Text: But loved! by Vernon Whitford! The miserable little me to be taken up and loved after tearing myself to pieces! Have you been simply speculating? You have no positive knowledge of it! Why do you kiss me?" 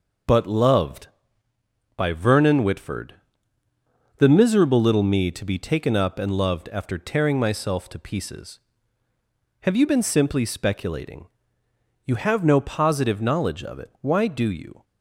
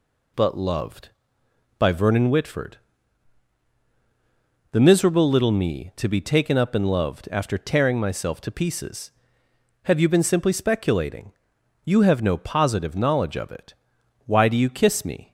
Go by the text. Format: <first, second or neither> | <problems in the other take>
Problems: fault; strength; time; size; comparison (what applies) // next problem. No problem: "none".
second | stops before "kiss me"; at 14.8 s